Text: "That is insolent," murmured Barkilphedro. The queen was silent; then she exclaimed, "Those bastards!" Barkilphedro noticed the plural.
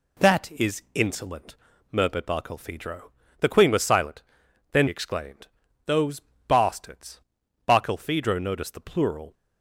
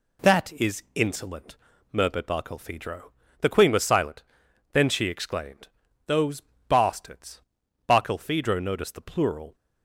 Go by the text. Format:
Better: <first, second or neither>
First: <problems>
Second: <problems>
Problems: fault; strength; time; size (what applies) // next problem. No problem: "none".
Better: second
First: skips "she"; at 4.8 s // pauses between "Those" and "bastards"; slight; at 6.2 s; 0.24 s long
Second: pauses between "Those" and "bastards"; slight; at 6.4 s; 0.24 s long